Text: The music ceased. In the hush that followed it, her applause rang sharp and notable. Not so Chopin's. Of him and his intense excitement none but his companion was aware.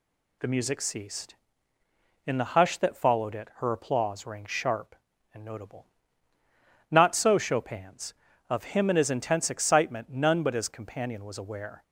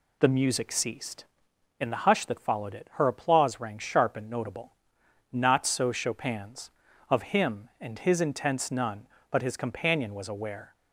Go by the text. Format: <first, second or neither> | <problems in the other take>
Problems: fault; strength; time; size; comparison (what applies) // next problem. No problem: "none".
first | skips "excitement"; at 8.7 s